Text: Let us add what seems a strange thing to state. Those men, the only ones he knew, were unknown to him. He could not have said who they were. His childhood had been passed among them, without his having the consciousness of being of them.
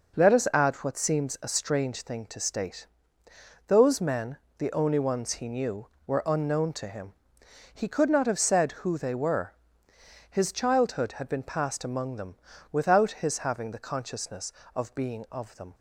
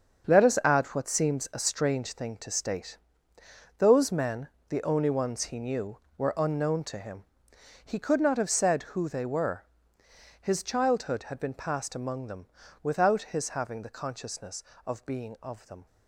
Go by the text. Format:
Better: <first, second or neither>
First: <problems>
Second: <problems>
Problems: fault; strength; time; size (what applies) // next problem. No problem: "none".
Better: first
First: none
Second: gets quieter; strong; throughout; 10.5 dB